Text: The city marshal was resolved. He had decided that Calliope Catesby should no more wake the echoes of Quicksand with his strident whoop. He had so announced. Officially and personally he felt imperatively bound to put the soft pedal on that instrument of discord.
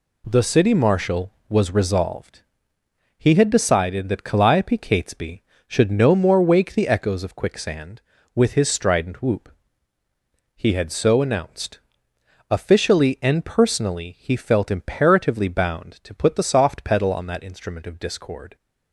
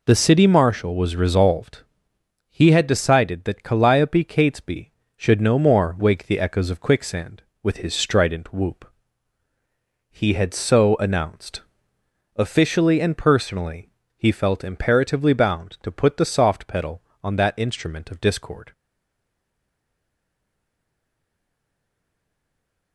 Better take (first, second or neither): first